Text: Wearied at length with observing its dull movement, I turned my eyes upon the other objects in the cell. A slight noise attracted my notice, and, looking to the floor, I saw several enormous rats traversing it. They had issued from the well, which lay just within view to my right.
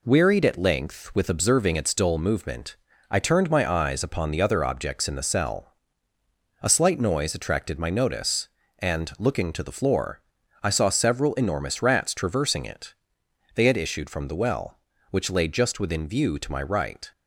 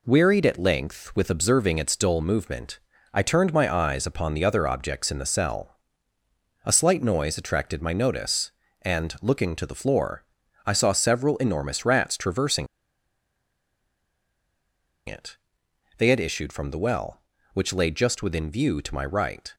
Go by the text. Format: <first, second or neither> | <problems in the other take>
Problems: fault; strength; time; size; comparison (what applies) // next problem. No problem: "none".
first | pauses between "traversing" and "it"; strong; at 12.6 s; 2.4 s long